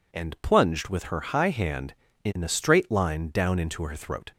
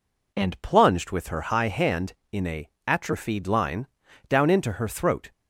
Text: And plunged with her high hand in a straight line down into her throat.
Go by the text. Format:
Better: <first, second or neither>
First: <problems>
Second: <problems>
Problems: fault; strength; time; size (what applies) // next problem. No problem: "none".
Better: first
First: none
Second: says "atrophied" for "straight"; at 2.8 s // pauses between "line" and "down"; at 3.8 s; 0.42 s long